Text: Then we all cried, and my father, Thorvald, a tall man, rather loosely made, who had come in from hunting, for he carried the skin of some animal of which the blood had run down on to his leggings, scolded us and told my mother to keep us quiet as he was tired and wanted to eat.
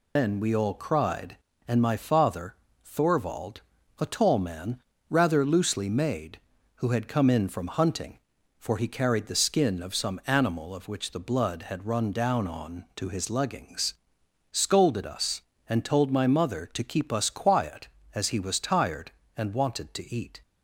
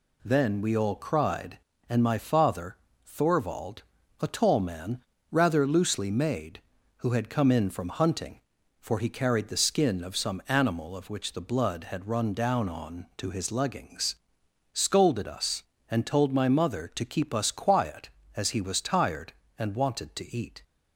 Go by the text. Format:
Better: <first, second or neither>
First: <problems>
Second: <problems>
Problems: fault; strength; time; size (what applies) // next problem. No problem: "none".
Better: second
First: loses the start of "Then"; at 0.1 s; 150 ms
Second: none